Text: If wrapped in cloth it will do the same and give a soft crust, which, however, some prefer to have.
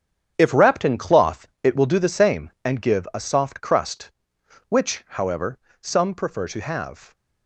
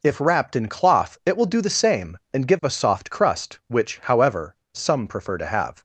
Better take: second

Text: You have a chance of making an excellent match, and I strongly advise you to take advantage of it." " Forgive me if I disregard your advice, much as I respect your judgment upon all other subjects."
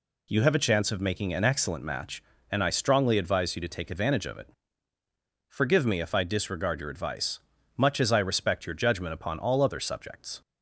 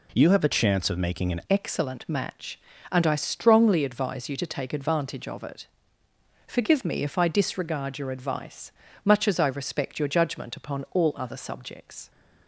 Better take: first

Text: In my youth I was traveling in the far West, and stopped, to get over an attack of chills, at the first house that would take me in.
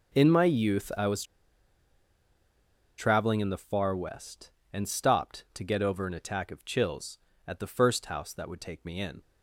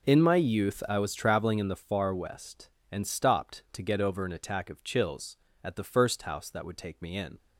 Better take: second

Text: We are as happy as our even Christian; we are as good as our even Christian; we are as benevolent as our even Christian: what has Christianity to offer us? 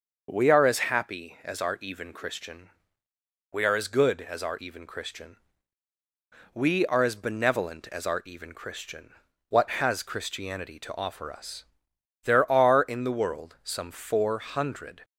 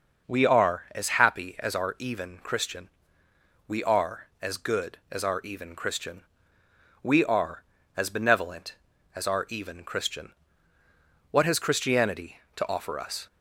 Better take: second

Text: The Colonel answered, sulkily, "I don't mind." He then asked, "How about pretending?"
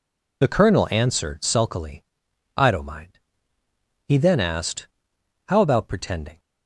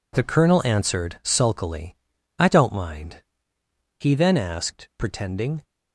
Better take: first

